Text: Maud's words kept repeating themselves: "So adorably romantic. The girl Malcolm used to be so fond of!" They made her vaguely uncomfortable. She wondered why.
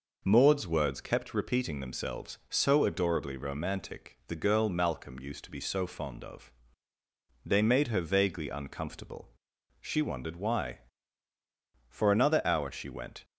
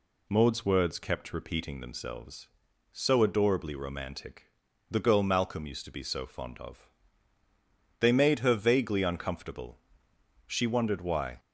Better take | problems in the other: second | goes on to say "For another hour she went"; from 11.8 s on; 1.3 s long

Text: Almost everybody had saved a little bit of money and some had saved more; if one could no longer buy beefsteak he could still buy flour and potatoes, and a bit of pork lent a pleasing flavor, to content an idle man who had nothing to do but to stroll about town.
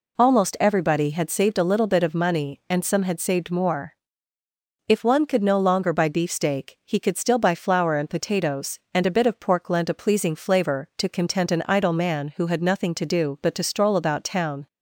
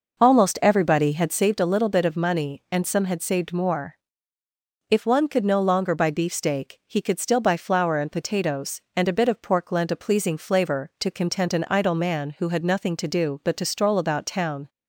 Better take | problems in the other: first | starts louder than the rest; noticeable; until 1.5 s; 5.5 dB

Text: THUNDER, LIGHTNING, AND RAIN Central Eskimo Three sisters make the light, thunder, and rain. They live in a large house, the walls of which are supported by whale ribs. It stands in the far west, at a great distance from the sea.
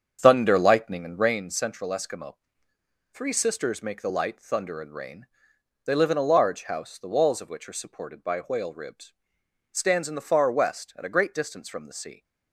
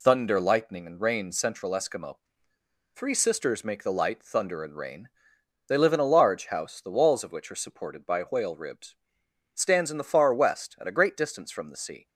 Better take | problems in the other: second | starts louder than the rest; strong; until 1.4 s; 7.5 dB // pauses between "Eskimo" and "Three"; noticeable; at 2.3 s; 0.78 s long; noticeable in the second

